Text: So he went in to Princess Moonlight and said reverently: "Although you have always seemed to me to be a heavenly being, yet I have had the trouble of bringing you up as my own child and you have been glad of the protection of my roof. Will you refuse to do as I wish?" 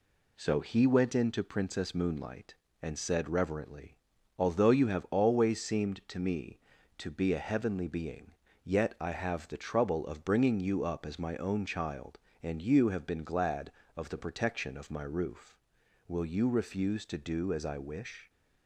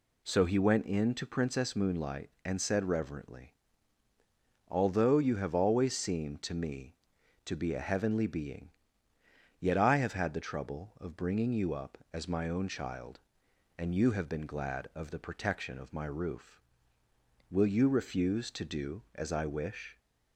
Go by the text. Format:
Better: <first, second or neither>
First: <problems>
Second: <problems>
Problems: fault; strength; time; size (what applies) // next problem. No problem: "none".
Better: second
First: skips "had"; at 9.4 s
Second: none